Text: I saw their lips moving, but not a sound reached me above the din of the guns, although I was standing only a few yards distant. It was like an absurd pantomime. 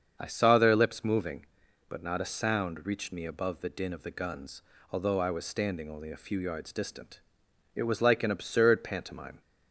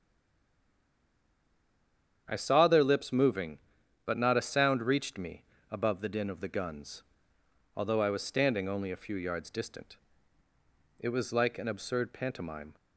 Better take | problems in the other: first | stays silent before the first word; until 2.2 s; 2.2 s long // starts louder than the rest; strong; until 3.2 s; 8.5 dB; strong in the first // pauses between "me" and "above"; slight; at 5.4 s; 0.26 s long

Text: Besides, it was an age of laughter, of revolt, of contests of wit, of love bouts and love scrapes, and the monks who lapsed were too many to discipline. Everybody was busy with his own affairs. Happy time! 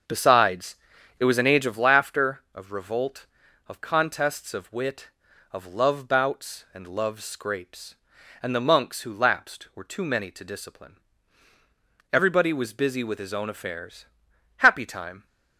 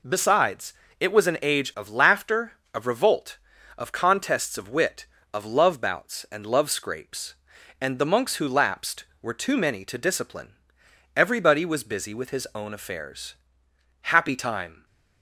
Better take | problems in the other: second | starts louder than the rest; until 1.9 s; 7 dB

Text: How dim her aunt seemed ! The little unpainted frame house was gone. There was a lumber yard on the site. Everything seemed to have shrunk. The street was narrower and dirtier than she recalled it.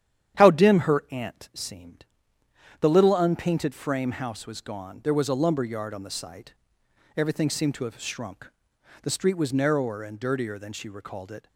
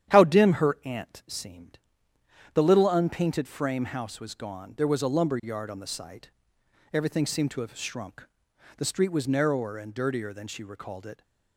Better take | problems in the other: neither | starts louder than the rest; strong; the same in both

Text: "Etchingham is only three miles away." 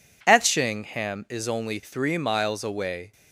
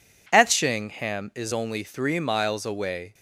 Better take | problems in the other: neither | none

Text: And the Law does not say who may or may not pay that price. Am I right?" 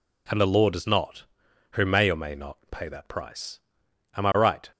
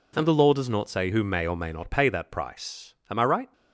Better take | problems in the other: second | skips "say"; at 1.4 s

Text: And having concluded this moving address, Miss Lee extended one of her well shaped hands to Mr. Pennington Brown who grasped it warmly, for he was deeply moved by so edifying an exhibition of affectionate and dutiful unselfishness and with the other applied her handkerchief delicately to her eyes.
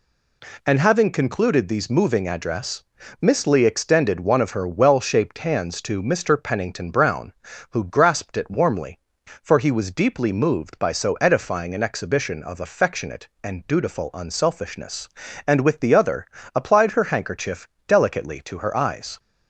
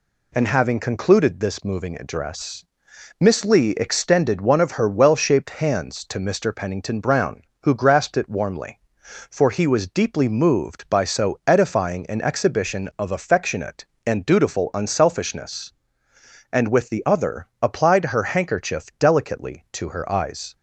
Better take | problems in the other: second | says "these" for "this"; at 1.6 s // pauses between "other" and "applied"; slight; at 16.2 s; 0.30 s long; slight in the second // pauses between "handkerchief" and "delicately"; slight; at 17.6 s; 0.22 s long

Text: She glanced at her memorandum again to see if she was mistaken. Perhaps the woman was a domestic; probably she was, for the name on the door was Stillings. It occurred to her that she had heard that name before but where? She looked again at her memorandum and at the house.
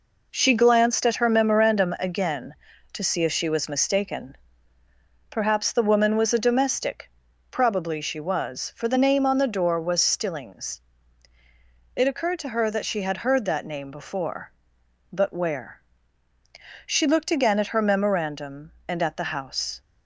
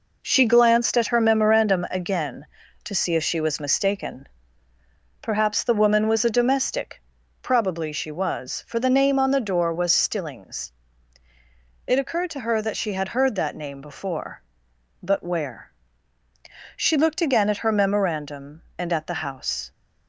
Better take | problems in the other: neither | none

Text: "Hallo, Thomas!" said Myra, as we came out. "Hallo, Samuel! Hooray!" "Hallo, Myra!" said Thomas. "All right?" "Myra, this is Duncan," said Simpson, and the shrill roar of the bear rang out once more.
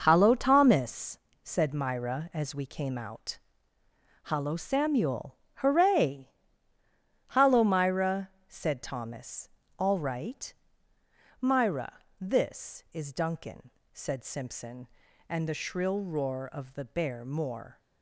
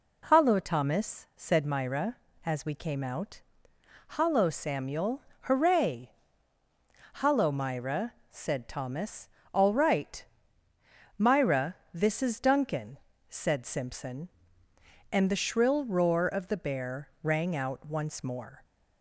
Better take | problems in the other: second | skips "rang out once"; at 17.2 s

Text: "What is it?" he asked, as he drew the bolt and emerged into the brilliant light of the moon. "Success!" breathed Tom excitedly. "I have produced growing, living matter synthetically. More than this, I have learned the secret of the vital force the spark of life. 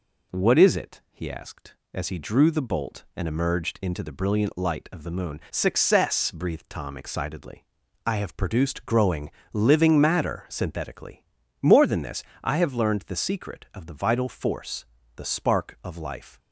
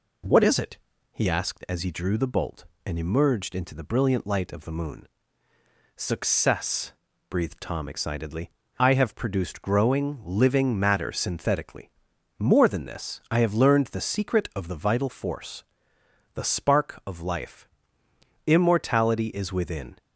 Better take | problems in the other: first | pauses between "force" and "the"; noticeable; at 15.6 s; 0.70 s long; slight in the first // goes on to say "Immortality is within"; from 18.4 s on; 1.5 s long

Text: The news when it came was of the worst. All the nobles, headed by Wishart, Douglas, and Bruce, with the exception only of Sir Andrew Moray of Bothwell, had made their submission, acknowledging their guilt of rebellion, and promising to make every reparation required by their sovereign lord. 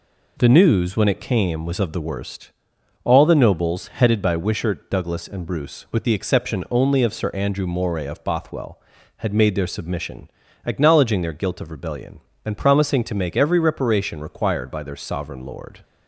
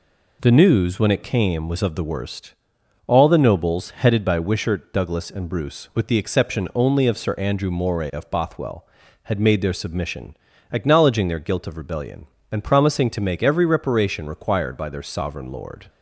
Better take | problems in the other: neither | none

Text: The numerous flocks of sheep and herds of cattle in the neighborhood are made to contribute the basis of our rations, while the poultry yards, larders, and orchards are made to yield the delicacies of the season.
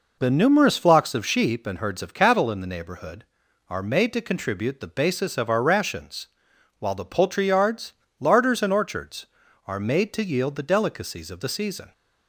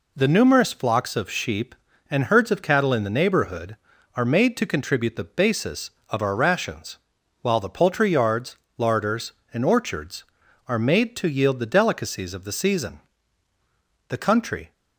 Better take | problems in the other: first | goes on to say "The country"; noticeable; from 14.0 s on; 0.64 s long

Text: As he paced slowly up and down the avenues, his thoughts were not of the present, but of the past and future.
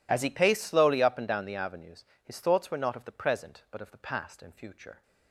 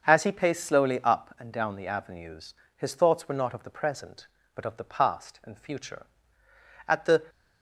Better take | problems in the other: first | starts louder than the rest; until 1.1 s; 6.5 dB // goes on to say "At the"; slight; from 6.8 s on; 0.34 s long

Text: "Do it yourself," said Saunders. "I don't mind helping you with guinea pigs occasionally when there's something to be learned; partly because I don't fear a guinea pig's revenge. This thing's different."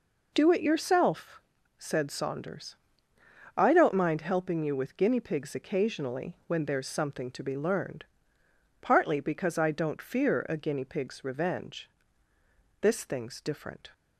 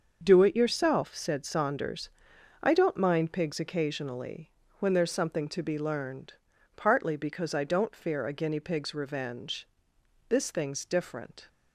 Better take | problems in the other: first | starts louder than the rest; until 1.2 s; 6.5 dB // skips "helping you with guinea"; at 3.3 s // pauses between "occasionally" and "when"; slight; at 4.5 s; 0.26 s long

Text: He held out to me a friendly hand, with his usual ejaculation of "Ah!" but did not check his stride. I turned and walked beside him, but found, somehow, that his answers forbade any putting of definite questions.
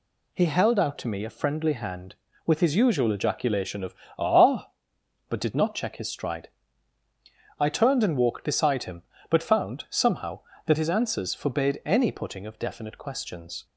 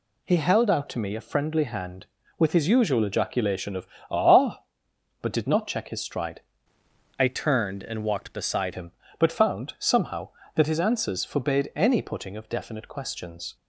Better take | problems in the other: first | pauses between "of" and "Ah"; slight; at 3.8 s; 0.22 s long; slight in the first // changes voice from "I" to "beside"; from 7.1 to 8.7 s; 1.6 s long

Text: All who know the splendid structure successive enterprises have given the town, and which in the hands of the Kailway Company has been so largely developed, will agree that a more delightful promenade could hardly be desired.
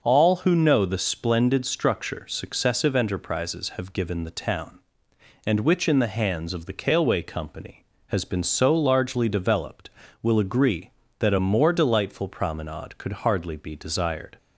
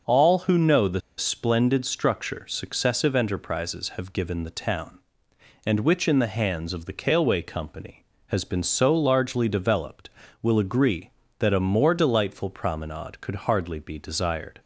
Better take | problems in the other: first | pauses between "the" and "splendid"; slight; at 1.0 s; 0.17 s long

